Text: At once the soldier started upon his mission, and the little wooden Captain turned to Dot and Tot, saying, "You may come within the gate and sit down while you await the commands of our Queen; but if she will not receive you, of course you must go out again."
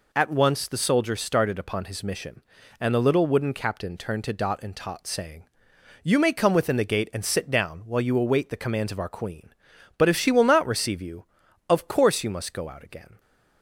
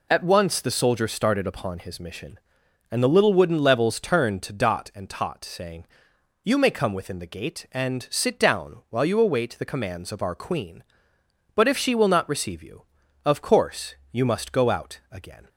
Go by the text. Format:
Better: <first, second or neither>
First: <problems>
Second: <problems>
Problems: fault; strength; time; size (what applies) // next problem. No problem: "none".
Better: first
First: none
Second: says "Levels" for "Captain"; at 3.5 s